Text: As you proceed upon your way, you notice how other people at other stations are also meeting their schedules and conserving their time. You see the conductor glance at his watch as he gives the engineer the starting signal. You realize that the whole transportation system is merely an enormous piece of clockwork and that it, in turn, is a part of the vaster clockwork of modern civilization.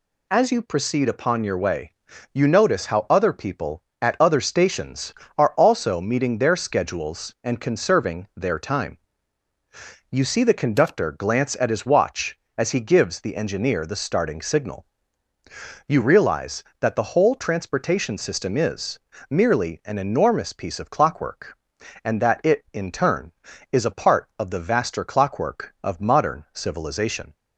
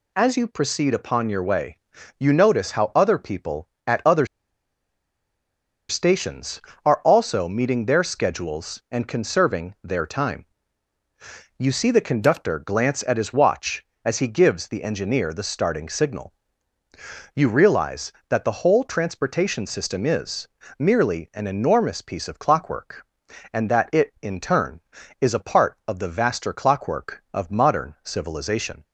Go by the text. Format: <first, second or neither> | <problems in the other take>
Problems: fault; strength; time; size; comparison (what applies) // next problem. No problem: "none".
first | pauses between "other" and "stations"; strong; at 4.2 s; 1.6 s long // pauses between "is" and "merely"; slight; at 20.4 s; 0.28 s long; slight in the first